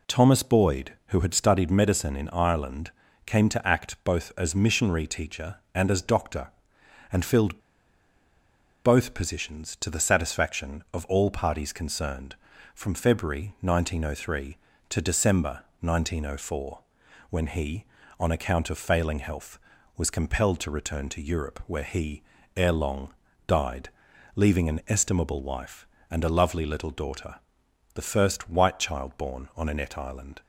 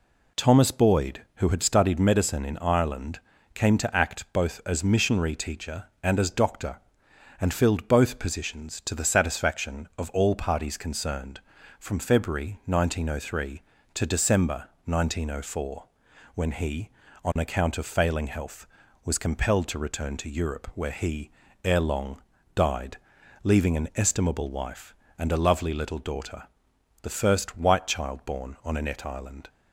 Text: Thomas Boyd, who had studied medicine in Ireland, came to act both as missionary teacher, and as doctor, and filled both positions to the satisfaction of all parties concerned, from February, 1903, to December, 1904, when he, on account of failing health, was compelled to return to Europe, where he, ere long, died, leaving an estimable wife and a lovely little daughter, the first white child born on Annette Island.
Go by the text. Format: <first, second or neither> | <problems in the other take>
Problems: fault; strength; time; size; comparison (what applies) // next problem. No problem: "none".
second | pauses between "filled" and "both"; strong; at 7.5 s; 1.2 s long